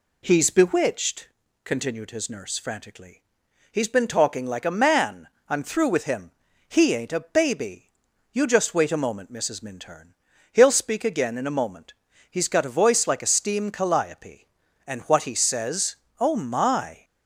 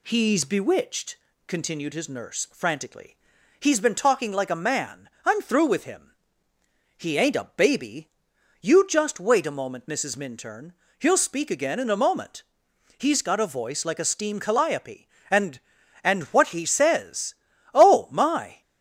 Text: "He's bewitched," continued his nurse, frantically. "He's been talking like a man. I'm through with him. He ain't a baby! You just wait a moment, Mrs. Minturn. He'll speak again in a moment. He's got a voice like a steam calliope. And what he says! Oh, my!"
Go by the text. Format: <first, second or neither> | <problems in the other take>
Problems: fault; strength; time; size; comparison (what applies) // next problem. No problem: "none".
first | says "And" twice; at 16.0 s